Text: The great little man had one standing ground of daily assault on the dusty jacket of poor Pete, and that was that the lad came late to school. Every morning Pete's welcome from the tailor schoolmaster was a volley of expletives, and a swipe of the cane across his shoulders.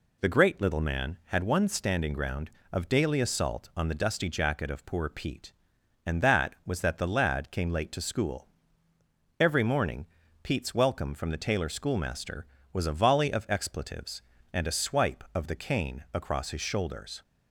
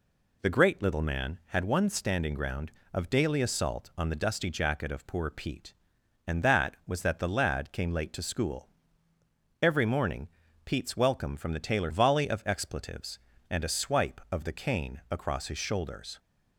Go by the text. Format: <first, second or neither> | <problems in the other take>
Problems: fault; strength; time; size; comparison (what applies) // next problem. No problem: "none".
first | pauses between "morning" and "Pete's"; slight; at 10.2 s; 0.34 s long; slight in the first // skips "schoolmaster was a"; at 11.9 s